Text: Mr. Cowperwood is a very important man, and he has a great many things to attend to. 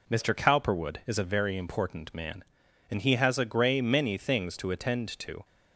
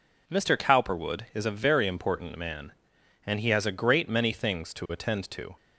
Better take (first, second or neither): second